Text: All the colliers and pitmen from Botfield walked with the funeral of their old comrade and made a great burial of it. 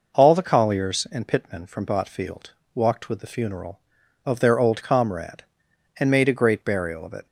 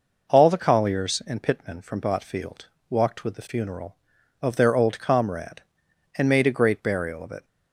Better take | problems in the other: neither | pauses between "Botfield" and "walked"; slight; the same in both

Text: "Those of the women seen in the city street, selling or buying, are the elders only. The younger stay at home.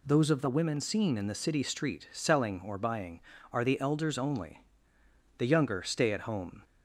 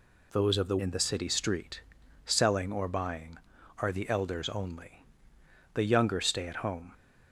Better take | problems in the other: first | skips "women seen"; at 0.7 s

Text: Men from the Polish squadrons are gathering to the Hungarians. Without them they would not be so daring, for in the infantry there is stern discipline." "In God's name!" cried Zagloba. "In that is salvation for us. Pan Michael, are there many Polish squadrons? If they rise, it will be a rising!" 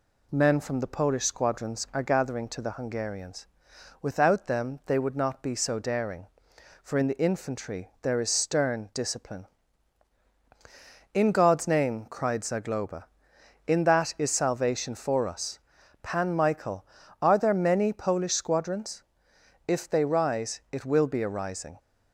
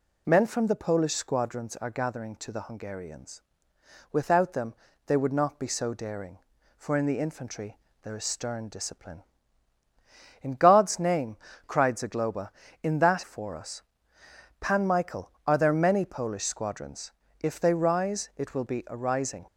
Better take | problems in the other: first | pauses between "them" and "they"; slight; at 4.7 s; 0.32 s long // pauses between "infantry" and "there"; slight; at 7.7 s; 0.24 s long // skips "is salvation"; at 13.2 s

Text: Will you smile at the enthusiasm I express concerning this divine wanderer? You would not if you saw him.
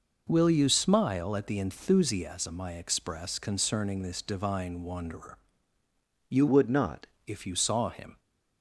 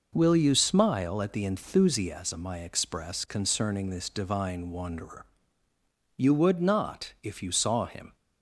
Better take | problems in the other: second | changes voice from "would" to "not"; from 6.4 to 7.0 s; 0.6 s long

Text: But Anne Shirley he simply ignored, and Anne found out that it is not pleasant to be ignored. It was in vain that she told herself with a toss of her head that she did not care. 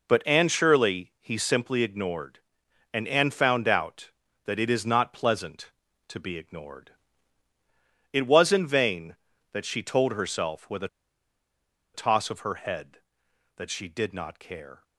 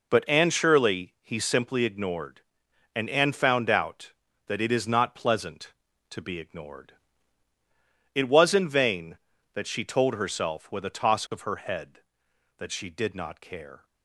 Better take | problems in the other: second | pauses between "a" and "toss"; at 10.8 s; 1.0 s long

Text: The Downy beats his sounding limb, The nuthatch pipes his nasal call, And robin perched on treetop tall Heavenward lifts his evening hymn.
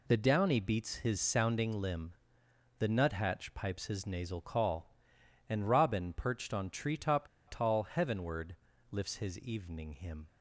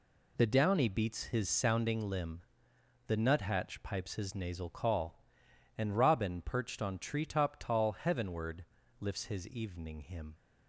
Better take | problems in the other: second | pauses between "treetop" and "tall"; slight; at 7.2 s; 0.20 s long // pauses between "Heavenward" and "lifts"; slight; at 8.5 s; 0.34 s long; slight in the second

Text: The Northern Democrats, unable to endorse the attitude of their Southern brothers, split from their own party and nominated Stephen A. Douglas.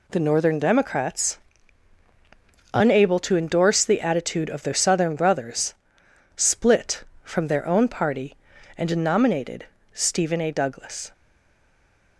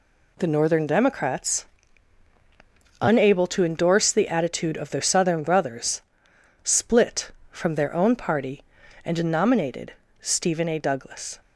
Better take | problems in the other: second | pauses between "nominated" and "Stephen"; slight; at 9.6 s; 0.30 s long; slight in the second // stays silent after the last word; from 11.1 s on; 1.0 s long

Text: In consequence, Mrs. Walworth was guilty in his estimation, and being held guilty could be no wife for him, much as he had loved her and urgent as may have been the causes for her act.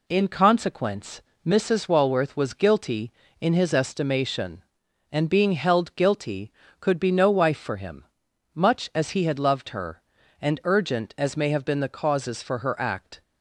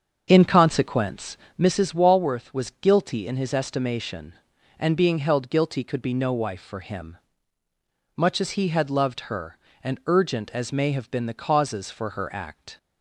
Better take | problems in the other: first | starts louder than the rest; until 1.7 s; 7 dB

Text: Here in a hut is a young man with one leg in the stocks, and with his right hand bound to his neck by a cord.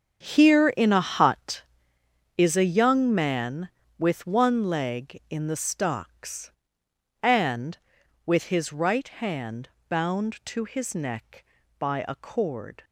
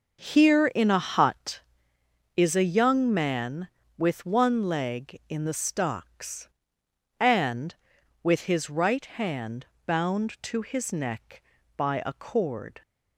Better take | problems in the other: second | gets quieter; strong; throughout; 13 dB // starts louder than the rest; strong; until 1.3 s; 7.5 dB; noticeable in the second // pauses between "hand" and "bound"; slight; at 9.7 s; 0.18 s long; slight in the second

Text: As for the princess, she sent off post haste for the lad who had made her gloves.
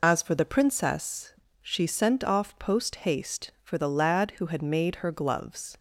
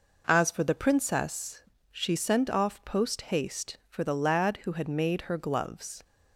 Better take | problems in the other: second | loses the start of "As"; at 0.0 s; 75 ms

